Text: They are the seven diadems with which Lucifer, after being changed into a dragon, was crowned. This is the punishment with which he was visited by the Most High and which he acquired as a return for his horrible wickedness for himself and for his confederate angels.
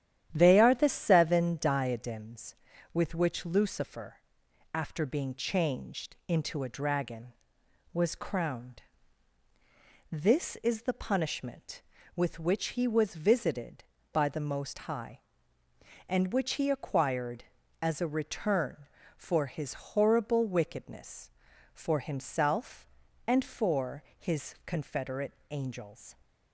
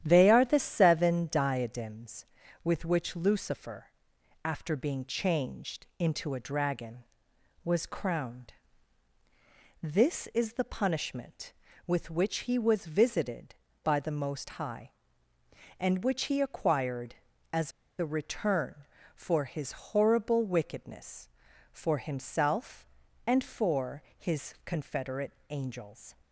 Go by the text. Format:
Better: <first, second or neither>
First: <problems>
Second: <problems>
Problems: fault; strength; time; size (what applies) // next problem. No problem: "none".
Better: first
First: starts louder than the rest; strong; until 1.3 s; 10.5 dB // pauses between "for" and "his"; slight; at 24.0 s; 0.16 s long // pauses between "confederate" and "angels"; slight; at 25.3 s; 0.16 s long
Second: starts louder than the rest; strong; until 1.0 s; 10.5 dB // pauses between "as" and "a"; slight; at 17.7 s; 0.27 s long // pauses between "for" and "his"; slight; at 24.0 s; 0.16 s long // pauses between "confederate" and "angels"; slight; at 25.3 s; 0.16 s long